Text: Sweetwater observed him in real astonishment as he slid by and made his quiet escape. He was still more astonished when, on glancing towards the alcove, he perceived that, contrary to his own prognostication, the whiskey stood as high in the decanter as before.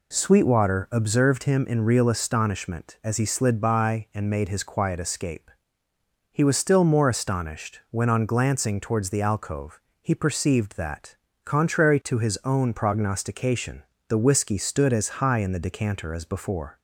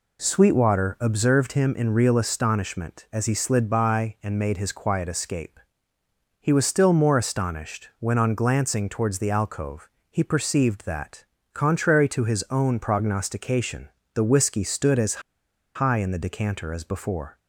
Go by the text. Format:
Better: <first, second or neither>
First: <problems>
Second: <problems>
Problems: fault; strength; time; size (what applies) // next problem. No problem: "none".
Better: first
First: none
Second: pauses between "as" and "high"; noticeable; at 15.2 s; 0.55 s long